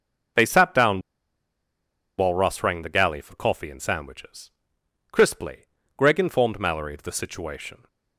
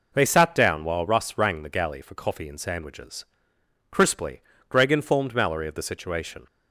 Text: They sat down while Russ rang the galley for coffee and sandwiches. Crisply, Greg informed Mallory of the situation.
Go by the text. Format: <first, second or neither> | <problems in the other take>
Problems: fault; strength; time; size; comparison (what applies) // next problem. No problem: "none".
second | pauses between "down" and "while"; at 0.9 s; 1.1 s long